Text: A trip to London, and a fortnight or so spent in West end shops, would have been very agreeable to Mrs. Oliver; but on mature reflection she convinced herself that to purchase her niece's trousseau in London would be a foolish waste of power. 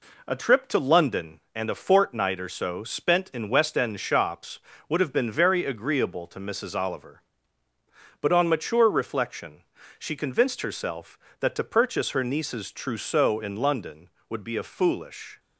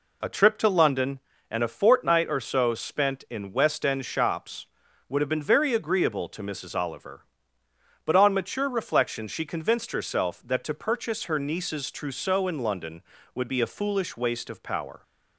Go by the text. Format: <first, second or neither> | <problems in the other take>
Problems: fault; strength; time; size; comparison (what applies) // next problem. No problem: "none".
second | pauses between "reflection" and "she"; at 9.6 s; 0.38 s long // stops before "waste of power"; at 15.3 s